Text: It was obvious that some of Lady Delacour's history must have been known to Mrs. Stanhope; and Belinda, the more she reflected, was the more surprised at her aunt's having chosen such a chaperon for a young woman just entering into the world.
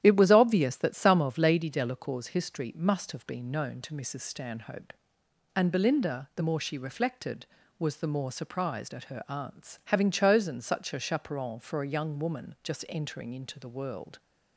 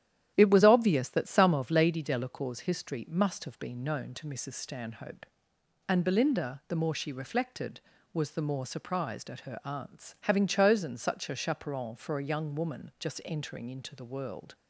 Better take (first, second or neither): neither